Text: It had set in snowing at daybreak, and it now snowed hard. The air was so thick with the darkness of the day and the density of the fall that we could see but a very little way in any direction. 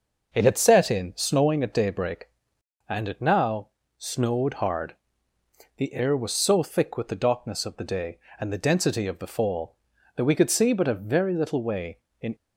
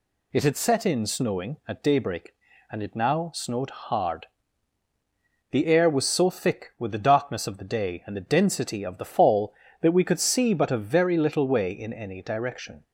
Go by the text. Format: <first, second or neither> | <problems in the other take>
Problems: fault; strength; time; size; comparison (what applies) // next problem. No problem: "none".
second | pauses between "now" and "snowed"; slight; at 3.6 s; 0.30 s long // stops before "any direction"; at 12.3 s